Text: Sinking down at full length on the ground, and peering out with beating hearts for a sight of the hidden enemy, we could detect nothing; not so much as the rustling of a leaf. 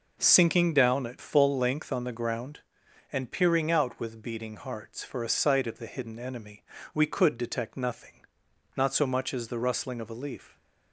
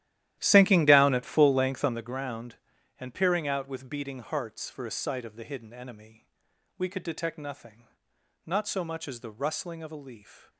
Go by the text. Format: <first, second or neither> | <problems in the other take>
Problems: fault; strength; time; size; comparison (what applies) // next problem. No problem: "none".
first | starts louder than the rest; strong; until 2.1 s; 13 dB